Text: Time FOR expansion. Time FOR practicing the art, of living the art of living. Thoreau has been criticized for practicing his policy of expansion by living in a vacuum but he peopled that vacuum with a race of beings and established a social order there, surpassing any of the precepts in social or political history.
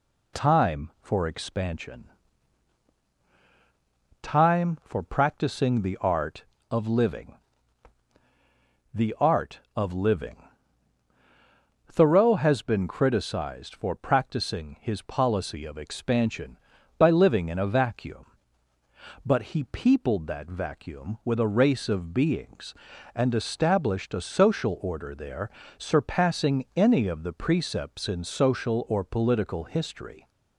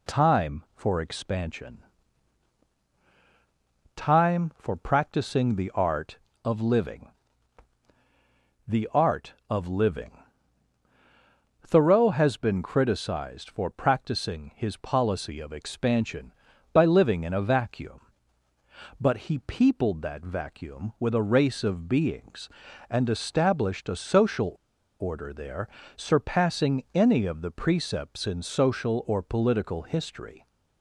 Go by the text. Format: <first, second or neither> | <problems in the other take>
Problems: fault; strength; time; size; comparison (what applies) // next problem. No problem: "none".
first | pauses between "living" and "the"; strong; at 7.0 s; 1.5 s long; strong in the first // pauses between "social" and "order"; noticeable; at 24.5 s; 0.46 s long